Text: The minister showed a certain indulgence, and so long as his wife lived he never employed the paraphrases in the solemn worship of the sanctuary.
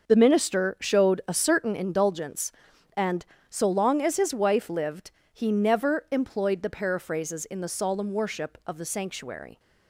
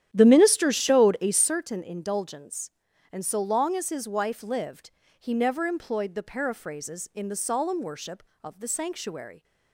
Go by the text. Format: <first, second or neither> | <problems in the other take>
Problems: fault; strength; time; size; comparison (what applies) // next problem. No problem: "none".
first | starts louder than the rest; strong; until 1.7 s; 10.5 dB // pauses between "lived" and "he"; slight; at 4.9 s; 0.30 s long; slight in the first